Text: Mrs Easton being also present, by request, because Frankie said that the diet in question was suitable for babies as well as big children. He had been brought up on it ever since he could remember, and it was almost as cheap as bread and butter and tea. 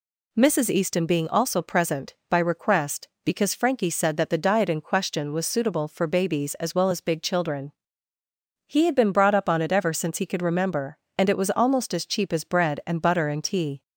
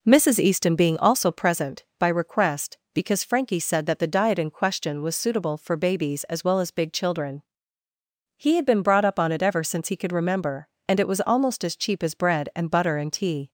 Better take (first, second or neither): first